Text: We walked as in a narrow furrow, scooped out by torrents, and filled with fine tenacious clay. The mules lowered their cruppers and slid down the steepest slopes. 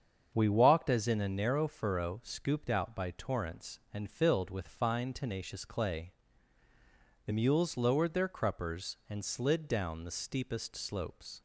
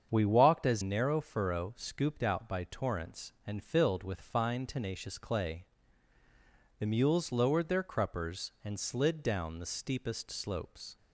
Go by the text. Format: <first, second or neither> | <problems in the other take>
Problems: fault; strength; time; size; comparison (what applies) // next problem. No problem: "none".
first | starts louder than the rest; strong; until 1.1 s; 7.5 dB; strong in the first // skips "in a"; at 0.8 s